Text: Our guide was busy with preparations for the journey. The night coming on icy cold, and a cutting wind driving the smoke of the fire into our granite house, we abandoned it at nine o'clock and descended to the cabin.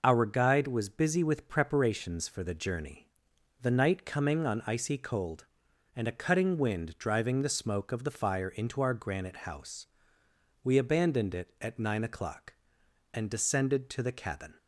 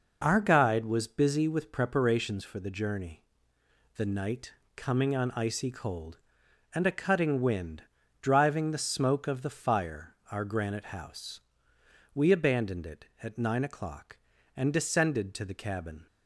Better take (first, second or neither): first